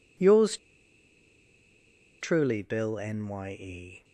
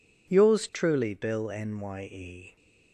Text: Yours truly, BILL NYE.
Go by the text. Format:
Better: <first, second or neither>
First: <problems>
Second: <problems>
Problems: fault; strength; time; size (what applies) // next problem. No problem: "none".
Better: second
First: pauses between "Yours" and "truly"; strong; at 0.5 s; 1.6 s long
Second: none